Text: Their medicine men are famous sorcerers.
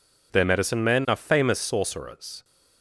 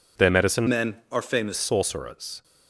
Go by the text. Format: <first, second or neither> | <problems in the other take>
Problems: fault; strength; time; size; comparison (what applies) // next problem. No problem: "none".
first | changes voice from "men" to "famous"; from 0.6 to 1.5 s; 0.9 s long